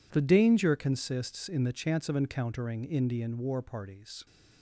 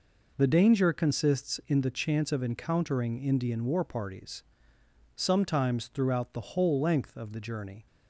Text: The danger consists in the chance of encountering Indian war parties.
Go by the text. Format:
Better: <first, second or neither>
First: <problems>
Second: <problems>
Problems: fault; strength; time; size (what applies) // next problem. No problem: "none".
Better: first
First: none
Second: goes on to say "Sometimes throughout the whole length of the journey"; strong; from 5.1 s on; 2.7 s long